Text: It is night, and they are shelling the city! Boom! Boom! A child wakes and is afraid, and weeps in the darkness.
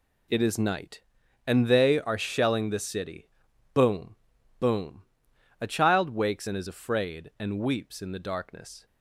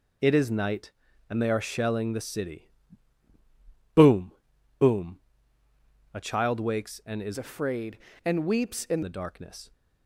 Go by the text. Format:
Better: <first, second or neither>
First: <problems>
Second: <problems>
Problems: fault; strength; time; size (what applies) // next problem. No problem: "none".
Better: first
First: none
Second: changes voice from "afraid" to "in"; from 7.3 to 9.0 s; 1.7 s long